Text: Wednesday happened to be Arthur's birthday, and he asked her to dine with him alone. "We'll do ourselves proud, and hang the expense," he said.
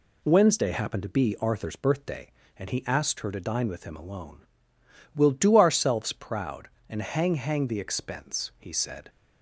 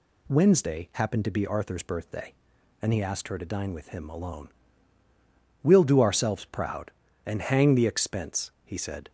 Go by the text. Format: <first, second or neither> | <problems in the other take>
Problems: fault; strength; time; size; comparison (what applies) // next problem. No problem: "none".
second | says "hang" twice; at 7.3 s